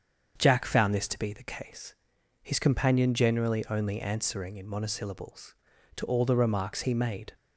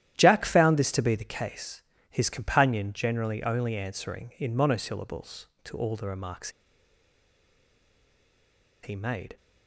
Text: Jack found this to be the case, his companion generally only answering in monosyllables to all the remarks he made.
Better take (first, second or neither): first